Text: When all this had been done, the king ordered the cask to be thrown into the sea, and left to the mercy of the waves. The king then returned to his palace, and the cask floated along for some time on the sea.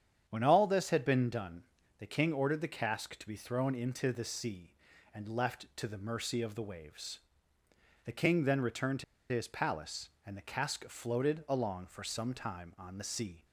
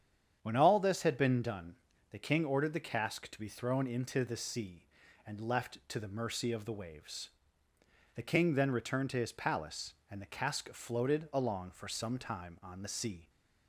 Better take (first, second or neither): second